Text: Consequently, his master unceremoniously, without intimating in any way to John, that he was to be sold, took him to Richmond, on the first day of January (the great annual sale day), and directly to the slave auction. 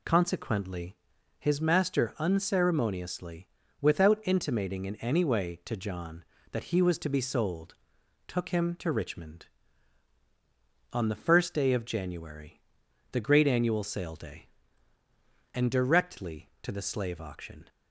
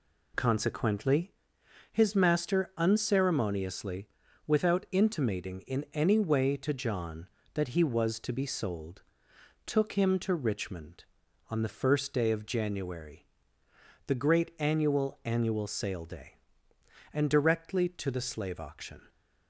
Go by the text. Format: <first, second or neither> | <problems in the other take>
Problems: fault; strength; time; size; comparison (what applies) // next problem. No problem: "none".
first | says "annual" twice; at 15.2 s